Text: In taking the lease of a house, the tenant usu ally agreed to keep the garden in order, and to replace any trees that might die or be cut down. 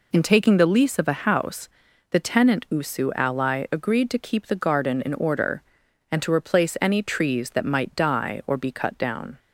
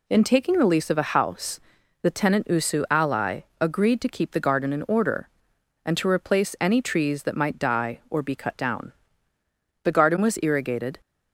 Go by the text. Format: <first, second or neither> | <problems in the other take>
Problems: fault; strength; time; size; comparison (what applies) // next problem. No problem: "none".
first | pauses between "ally" and "agreed"; slight; at 3.3 s; 0.20 s long // goes on to say "The garden was irrigated"; noticeable; from 9.8 s on; 1.1 s long